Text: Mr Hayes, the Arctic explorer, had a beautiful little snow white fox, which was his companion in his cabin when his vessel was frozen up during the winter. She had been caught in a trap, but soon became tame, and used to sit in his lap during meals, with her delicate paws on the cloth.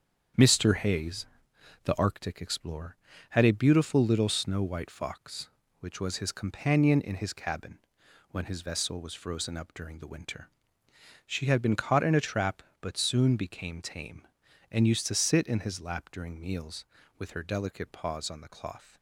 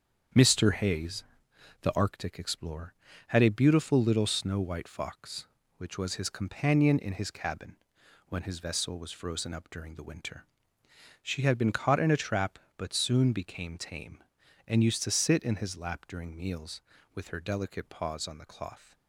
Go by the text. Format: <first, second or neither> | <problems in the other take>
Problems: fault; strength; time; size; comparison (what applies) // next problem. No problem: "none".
neither | starts louder than the rest; strong; the same in both // pauses between "cabin" and "when"; noticeable; the same in both